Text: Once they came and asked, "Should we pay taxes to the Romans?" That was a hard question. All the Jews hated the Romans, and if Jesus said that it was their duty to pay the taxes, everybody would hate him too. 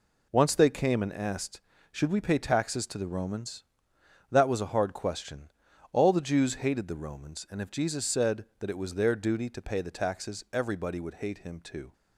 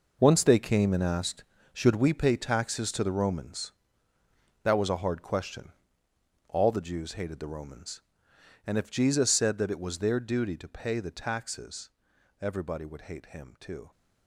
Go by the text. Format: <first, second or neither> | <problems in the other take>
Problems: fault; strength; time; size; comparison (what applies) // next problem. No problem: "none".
first | gets quieter; strong; throughout; 11.5 dB